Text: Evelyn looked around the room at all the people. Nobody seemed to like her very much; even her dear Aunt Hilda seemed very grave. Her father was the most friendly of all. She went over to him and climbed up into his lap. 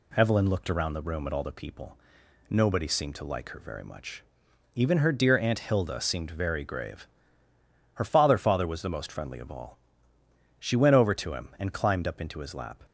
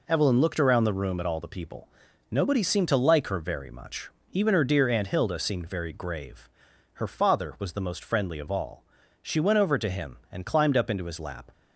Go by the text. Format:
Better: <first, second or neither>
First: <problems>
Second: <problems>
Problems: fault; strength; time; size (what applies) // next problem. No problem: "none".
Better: second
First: says "father" twice; at 8.3 s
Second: none